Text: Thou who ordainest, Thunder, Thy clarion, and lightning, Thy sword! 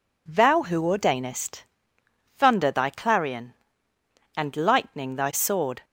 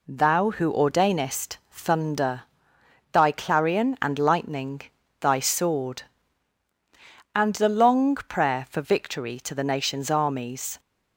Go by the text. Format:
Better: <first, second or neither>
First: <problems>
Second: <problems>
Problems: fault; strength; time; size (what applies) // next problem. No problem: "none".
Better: first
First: none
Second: goes on to say "and the long prayer for victory to the nation's armies"; strong; from 7.3 s on; 3.4 s long